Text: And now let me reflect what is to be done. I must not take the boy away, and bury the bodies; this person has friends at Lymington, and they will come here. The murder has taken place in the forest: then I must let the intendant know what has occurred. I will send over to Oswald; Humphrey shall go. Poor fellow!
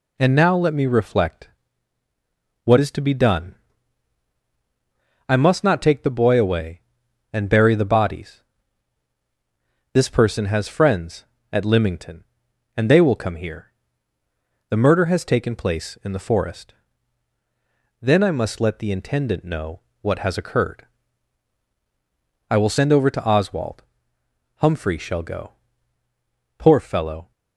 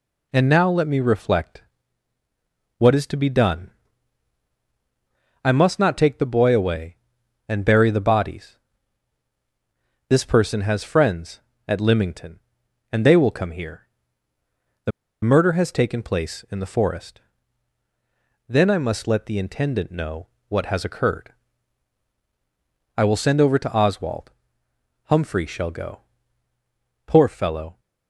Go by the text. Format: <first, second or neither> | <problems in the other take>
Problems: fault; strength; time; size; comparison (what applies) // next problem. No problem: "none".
first | pauses between "reflect" and "what"; at 1.6 s; 1.1 s long; also in the first // pauses between "The" and "murder"; slight; at 14.9 s; 0.32 s long // pauses between "know" and "what"; slight; at 20.2 s; 0.22 s long; slight in the first